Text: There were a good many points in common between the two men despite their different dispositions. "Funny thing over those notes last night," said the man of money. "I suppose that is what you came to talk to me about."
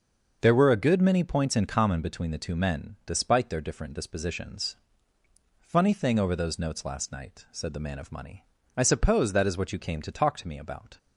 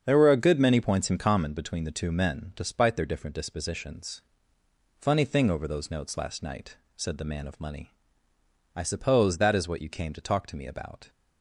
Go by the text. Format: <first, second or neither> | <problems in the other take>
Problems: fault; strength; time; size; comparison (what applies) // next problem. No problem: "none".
neither | starts louder than the rest; the same in both